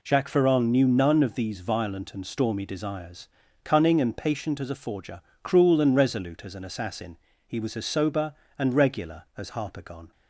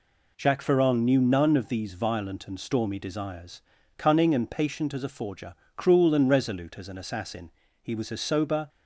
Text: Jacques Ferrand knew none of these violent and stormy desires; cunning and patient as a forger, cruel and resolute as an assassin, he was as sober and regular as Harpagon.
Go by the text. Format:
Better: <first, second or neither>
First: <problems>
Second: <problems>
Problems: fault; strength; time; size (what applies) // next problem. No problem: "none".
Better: first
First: none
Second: stops before "and regular as Harpagon"; at 8.6 s